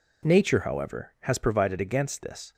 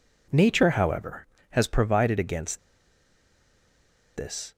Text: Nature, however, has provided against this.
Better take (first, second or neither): first